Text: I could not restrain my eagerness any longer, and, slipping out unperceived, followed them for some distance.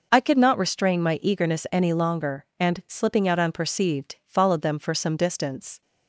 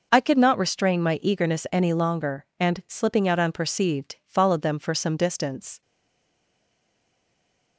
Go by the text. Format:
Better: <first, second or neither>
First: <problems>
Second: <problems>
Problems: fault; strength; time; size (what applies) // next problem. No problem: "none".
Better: first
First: none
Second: stays silent after the last word; noticeable; from 5.8 s on; 1.9 s long